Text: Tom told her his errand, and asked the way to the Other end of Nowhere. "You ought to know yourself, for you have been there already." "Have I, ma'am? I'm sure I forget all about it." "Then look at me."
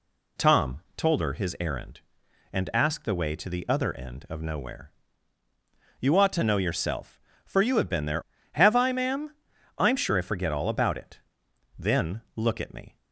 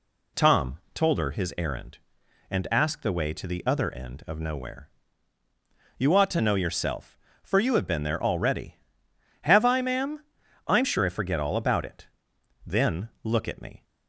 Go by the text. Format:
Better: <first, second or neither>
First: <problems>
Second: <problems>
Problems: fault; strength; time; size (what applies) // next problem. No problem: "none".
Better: second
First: skips "already"; at 8.3 s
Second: none